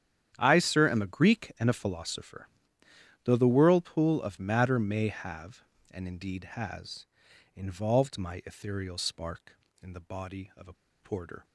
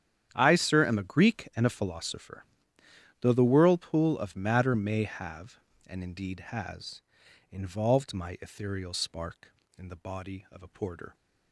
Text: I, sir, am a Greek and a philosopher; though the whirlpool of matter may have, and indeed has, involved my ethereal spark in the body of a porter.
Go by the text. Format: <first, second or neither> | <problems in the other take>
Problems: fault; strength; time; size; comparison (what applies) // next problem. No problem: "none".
second | starts louder than the rest; strong; until 1.3 s; 9.5 dB; strong in the second // pauses between "a" and "porter"; slight; at 10.7 s; 0.26 s long